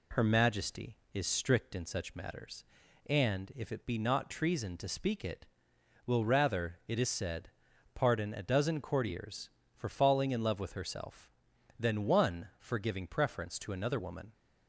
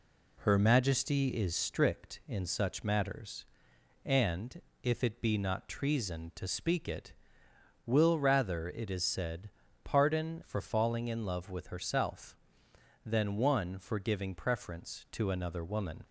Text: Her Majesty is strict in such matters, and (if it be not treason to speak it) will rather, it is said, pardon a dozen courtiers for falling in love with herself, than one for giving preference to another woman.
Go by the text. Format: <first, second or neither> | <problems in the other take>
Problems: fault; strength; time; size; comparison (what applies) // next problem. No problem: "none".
first | skips "a dozen courtiers"; at 10.4 s